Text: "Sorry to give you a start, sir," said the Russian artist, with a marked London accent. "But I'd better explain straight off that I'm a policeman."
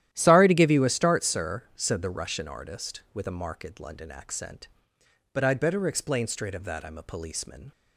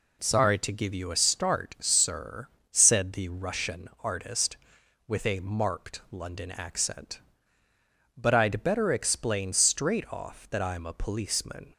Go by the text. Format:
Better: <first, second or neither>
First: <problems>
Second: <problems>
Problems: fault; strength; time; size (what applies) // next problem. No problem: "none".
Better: second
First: starts louder than the rest; strong; until 1.1 s; 12 dB // says "of" for "off"; at 6.5 s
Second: none